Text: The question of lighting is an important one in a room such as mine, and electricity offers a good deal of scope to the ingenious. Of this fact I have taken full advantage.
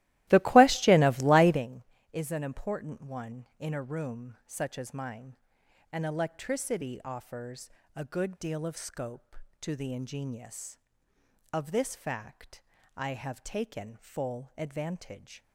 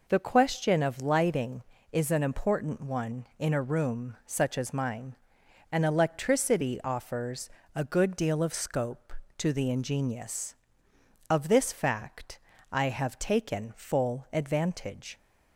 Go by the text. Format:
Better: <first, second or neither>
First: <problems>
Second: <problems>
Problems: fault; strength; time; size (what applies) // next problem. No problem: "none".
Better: second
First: starts louder than the rest; strong; until 1.6 s; 16.5 dB // pauses between "offers" and "a"; slight; at 7.6 s; 0.26 s long // pauses between "fact" and "I"; slight; at 12.6 s; 0.34 s long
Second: pauses between "offers" and "a"; slight; at 7.4 s; 0.26 s long // pauses between "fact" and "I"; slight; at 12.3 s; 0.32 s long